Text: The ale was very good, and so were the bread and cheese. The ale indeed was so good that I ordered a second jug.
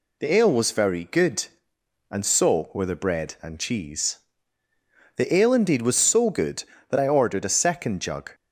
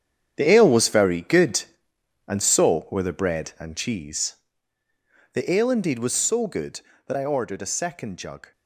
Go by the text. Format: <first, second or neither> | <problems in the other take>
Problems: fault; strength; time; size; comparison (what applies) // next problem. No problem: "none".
first | gets quieter; strong; throughout; 11.5 dB